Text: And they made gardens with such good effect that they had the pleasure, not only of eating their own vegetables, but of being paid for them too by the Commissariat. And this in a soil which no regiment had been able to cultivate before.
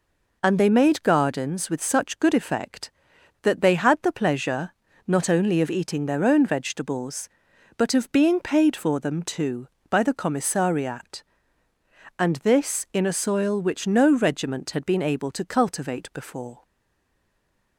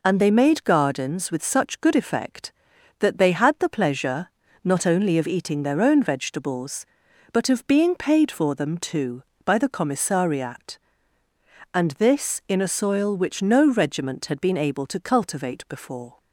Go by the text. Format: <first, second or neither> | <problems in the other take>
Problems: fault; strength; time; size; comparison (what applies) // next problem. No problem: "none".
second | stays silent after the last word; noticeable; from 16.6 s on; 1.1 s long